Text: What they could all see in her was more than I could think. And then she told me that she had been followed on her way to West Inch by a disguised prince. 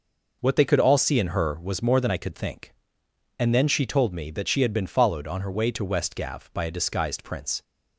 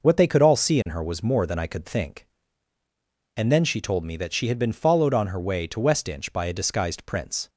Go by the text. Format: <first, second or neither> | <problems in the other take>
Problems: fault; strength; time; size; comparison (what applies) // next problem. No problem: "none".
second | says "Gav" for "Inch"; at 6.1 s